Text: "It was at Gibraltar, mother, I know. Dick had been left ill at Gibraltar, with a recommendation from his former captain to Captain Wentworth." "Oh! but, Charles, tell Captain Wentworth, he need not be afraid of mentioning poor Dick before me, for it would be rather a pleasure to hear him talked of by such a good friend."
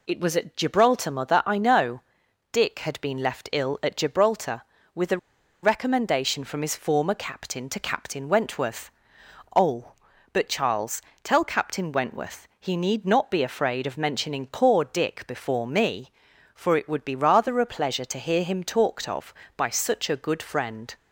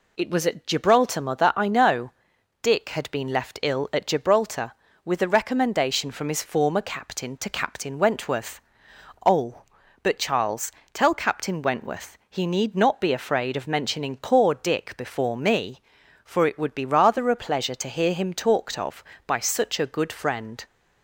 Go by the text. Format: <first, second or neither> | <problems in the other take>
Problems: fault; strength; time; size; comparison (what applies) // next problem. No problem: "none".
second | pauses between "a" and "recommendation"; at 5.1 s; 0.45 s long